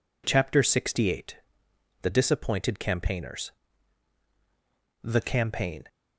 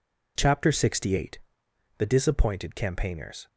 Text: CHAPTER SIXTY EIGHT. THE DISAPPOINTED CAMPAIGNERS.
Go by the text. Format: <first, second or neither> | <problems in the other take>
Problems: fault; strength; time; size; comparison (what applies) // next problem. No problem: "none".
second | goes on to say "The campaign"; noticeable; from 5.0 s on; 0.82 s long